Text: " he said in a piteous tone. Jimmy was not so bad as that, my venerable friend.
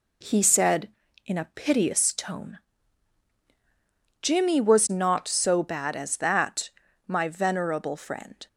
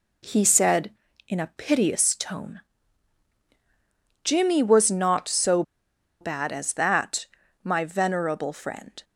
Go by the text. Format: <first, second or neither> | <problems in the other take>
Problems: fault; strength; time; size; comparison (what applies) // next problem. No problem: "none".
first | pauses between "so" and "bad"; noticeable; at 5.6 s; 0.58 s long